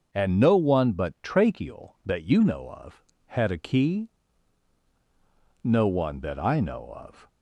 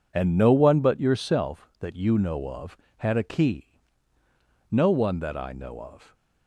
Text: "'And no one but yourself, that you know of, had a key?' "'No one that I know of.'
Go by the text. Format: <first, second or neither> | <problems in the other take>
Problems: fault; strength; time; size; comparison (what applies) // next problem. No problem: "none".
second | starts louder than the rest; until 1.1 s; 6.5 dB // says "tracheal" for "yourself"; at 1.2 s